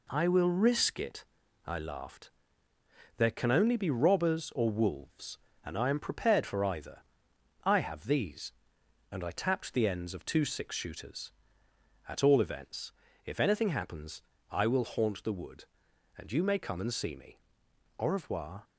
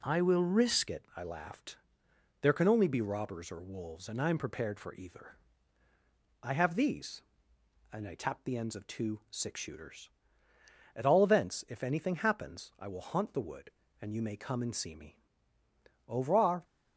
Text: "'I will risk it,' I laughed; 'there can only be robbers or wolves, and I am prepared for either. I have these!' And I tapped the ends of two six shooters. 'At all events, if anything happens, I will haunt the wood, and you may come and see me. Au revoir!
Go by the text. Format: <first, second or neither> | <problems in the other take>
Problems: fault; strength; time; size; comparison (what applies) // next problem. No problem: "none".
first | changes voice at "it"; from 0.8 s on; 15.8 s long